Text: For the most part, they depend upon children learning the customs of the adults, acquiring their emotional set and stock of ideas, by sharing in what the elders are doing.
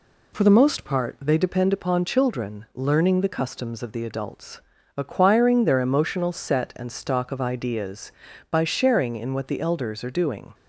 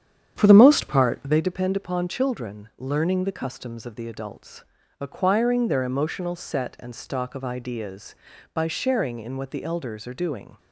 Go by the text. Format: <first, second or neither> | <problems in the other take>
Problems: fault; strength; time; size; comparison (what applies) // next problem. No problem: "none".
first | starts louder than the rest; strong; until 1.4 s; 9 dB